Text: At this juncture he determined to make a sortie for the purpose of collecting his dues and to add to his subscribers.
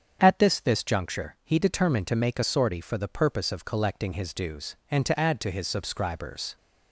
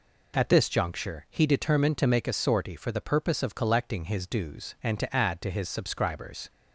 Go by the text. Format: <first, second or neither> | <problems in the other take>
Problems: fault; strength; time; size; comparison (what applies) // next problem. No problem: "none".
second | starts louder than the rest; strong; until 1.2 s; 7.5 dB // says "this" twice; at 0.6 s